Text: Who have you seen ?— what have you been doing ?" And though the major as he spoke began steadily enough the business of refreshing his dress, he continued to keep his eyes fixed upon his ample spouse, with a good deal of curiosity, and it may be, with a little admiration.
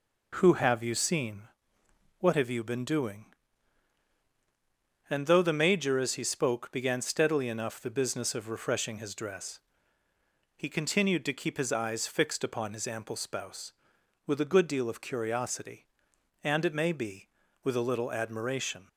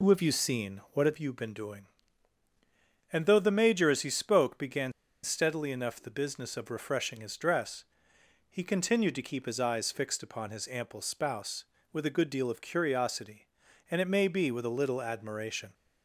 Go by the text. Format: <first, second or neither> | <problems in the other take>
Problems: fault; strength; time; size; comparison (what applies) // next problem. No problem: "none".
first | pauses between "began" and "steadily"; slight; at 4.9 s; 0.31 s long